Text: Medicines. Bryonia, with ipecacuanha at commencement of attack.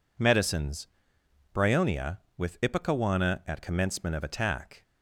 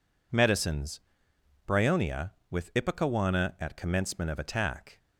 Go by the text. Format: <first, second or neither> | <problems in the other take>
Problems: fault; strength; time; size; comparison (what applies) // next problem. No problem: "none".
neither | none